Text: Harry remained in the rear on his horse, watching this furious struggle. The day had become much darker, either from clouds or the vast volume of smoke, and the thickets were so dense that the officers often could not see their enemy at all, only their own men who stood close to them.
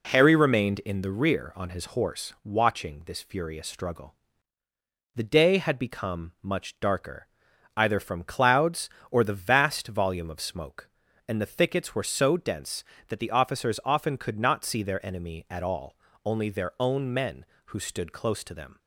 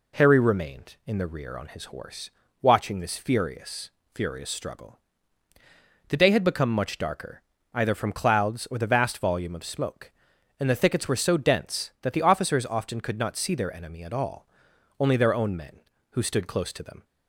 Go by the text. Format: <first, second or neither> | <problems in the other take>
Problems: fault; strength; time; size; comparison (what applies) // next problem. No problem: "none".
first | says "furious" twice; at 4.1 s